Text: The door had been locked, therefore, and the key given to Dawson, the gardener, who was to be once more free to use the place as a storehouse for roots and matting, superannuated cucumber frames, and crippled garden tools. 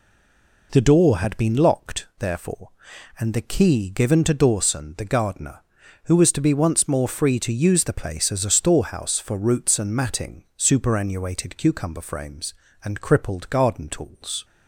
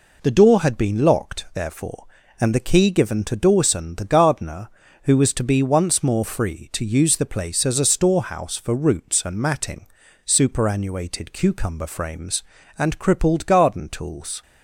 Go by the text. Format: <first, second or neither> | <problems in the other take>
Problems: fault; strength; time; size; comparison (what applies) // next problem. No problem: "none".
second | stays silent before the first word; slight; until 0.7 s; 0.7 s long